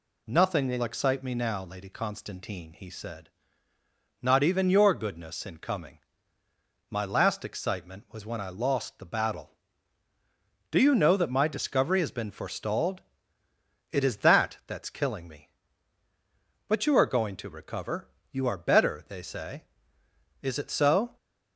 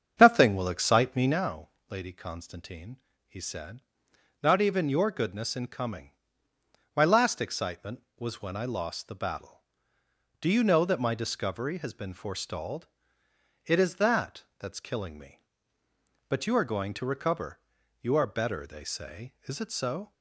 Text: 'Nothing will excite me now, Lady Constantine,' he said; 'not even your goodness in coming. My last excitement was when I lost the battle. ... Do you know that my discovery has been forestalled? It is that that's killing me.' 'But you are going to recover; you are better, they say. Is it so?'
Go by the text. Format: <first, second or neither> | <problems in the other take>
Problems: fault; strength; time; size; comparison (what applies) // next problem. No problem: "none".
first | starts louder than the rest; strong; until 1.4 s; 7.5 dB